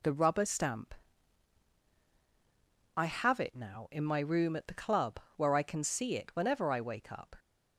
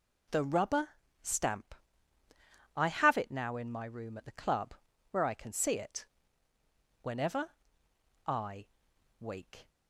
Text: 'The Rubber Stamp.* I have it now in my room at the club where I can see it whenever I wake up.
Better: first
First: pauses between "club" and "where"; slight; at 5.1 s; 0.16 s long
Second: pauses between "Rubber" and "Stamp"; slight; at 0.8 s; 0.34 s long // pauses between "club" and "where"; slight; at 4.7 s; 0.36 s long // pauses between "it" and "whenever"; noticeable; at 6.0 s; 0.96 s long // pauses between "whenever" and "I"; noticeable; at 7.5 s; 0.76 s long // pauses between "I" and "wake"; noticeable; at 8.6 s; 0.52 s long // stops before "up"; at 9.6 s

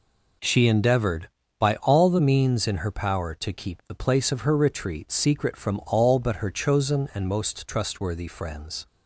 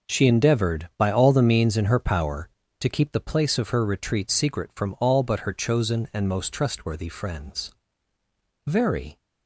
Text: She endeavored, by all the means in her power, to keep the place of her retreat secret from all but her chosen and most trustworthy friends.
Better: first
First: none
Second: goes on to say "Very"; from 8.6 s on; 0.52 s long

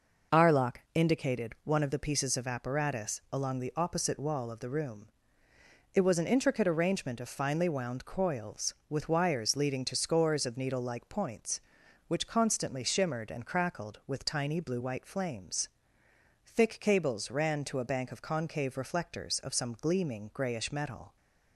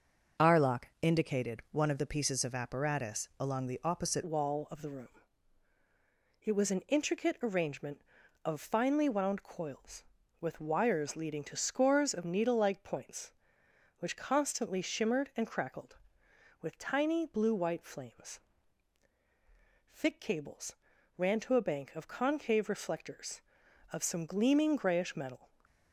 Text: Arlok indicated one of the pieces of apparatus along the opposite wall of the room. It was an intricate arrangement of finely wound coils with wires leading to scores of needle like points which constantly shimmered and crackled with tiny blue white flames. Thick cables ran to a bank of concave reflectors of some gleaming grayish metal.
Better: first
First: none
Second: changes voice at "wall"; from 4.2 s on; 21.2 s long // pauses between "cables" and "ran"; at 20.7 s; 0.40 s long

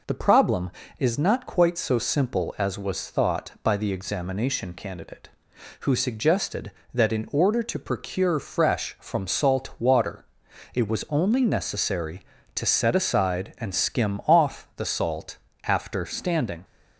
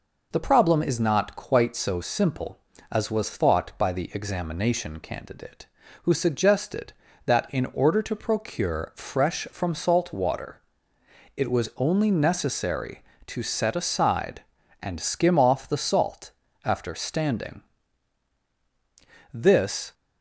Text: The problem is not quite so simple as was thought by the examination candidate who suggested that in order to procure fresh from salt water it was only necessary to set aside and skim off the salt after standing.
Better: first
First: pauses between "water" and "it"; noticeable; at 10.2 s; 0.50 s long // pauses between "salt" and "after"; slight; at 15.3 s; 0.26 s long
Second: pauses between "water" and "it"; noticeable; at 10.6 s; 0.74 s long // pauses between "salt" and "after"; slight; at 16.3 s; 0.32 s long // goes on to say "This"; from 19.3 s on; 0.60 s long

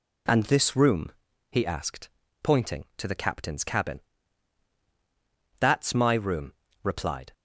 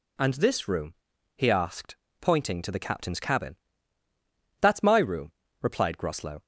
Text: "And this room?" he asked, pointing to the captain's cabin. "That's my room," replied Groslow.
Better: second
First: stops before "Groslow"; at 7.3 s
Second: none

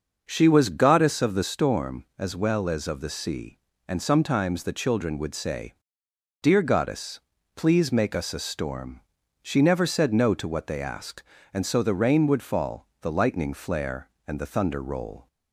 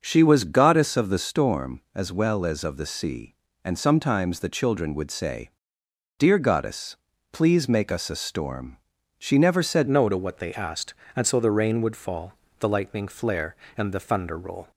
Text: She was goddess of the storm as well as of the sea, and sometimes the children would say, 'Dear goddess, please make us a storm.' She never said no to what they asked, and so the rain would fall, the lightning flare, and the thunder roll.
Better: first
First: starts louder than the rest; until 1.2 s; 6.5 dB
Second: starts louder than the rest; until 1.0 s; 6.5 dB // changes voice at "no"; from 9.8 s on; 4.9 s long

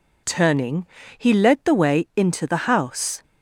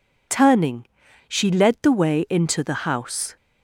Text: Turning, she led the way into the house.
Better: second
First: says "he" for "she"; at 1.1 s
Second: none

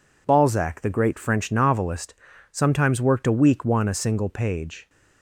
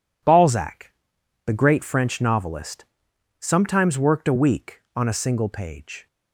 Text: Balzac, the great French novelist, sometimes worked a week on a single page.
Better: second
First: says "one" for "on"; at 3.6 s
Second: none

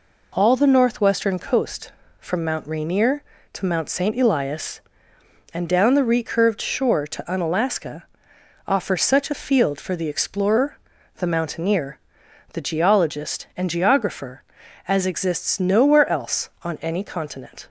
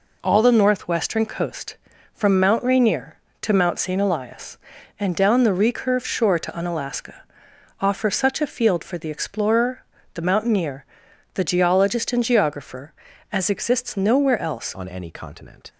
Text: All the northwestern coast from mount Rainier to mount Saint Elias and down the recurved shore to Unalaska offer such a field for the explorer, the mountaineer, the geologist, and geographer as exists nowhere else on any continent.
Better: first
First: pauses between "Unalaska" and "offer"; noticeable; at 8.0 s; 0.62 s long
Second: pauses between "Unalaska" and "offer"; noticeable; at 7.2 s; 0.58 s long // changes voice at "on"; from 14.7 s on; 1.0 s long

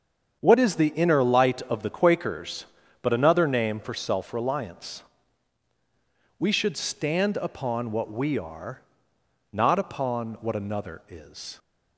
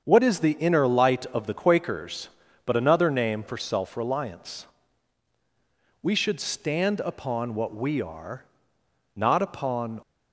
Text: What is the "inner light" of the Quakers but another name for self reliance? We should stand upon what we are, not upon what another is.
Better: first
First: starts louder than the rest; strong; until 1.4 s; 7.5 dB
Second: starts louder than the rest; strong; until 1.0 s; 7 dB // stops before "what another is"; at 10.0 s

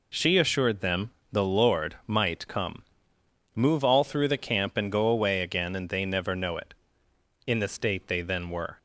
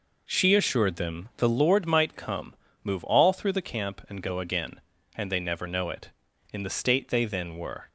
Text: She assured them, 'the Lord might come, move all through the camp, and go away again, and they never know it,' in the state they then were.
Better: first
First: none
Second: skips "away"; at 4.3 s

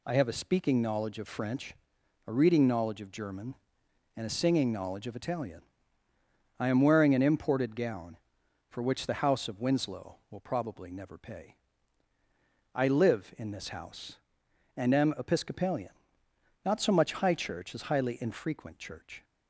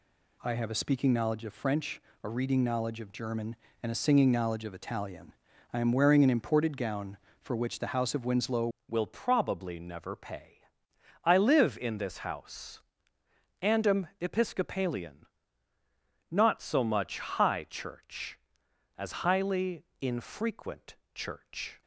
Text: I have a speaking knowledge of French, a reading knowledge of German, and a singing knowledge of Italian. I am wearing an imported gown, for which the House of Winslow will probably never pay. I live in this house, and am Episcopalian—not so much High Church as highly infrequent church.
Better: first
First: none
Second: changes voice at "will"; from 8.8 s on; 13.0 s long // pauses between "highly" and "infrequent"; slight; at 19.8 s; 0.16 s long // pauses between "infrequent" and "church"; slight; at 20.9 s; 0.18 s long

